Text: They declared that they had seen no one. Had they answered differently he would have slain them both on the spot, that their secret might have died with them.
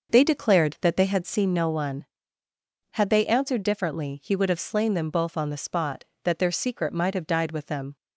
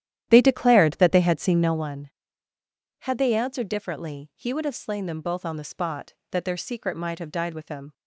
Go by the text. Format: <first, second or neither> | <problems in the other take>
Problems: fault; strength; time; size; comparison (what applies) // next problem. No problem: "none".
first | starts louder than the rest; strong; until 1.9 s; 11.5 dB